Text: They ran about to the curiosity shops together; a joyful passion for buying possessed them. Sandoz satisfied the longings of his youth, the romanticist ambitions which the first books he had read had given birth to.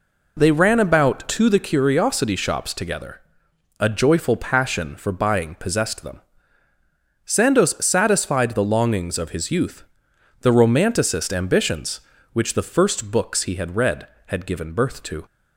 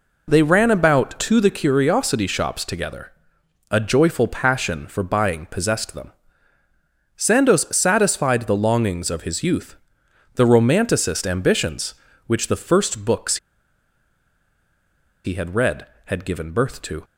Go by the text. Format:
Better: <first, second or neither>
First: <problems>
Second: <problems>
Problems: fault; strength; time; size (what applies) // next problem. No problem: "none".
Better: first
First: none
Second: pauses between "books" and "he"; strong; at 13.3 s; 1.8 s long